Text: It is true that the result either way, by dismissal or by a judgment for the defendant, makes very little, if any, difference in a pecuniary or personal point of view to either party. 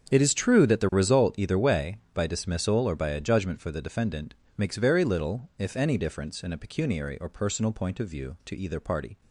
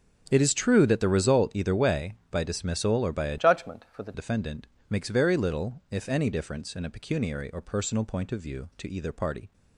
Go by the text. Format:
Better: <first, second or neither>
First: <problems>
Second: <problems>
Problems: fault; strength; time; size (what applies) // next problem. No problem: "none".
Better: first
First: starts louder than the rest; strong; until 1.1 s; 8 dB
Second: starts louder than the rest; until 1.3 s; 6.5 dB // changes voice from "judgment" to "the"; from 3.3 to 4.1 s; 0.8 s long